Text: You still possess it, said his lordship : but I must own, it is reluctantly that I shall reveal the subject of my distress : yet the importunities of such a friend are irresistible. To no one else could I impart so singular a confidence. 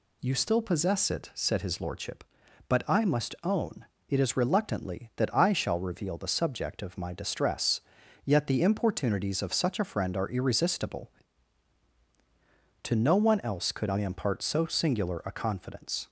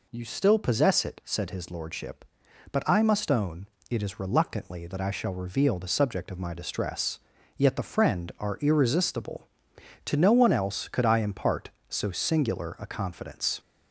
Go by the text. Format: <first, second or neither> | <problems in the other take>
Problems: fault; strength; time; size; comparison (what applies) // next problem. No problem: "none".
first | skips "importunities of such a"; at 7.8 s